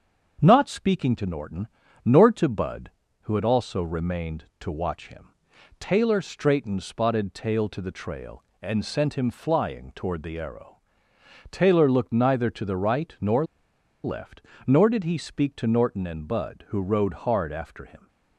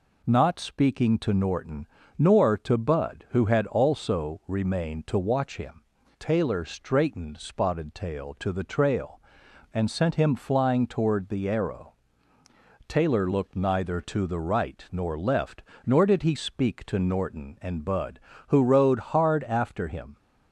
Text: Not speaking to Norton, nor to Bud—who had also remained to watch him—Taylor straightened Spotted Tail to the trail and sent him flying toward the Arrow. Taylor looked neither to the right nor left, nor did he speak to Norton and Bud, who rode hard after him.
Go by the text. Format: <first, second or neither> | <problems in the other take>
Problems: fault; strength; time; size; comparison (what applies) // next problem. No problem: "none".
second | starts louder than the rest; until 1.4 s; 7 dB // pauses between "nor" and "left"; noticeable; at 13.4 s; 0.60 s long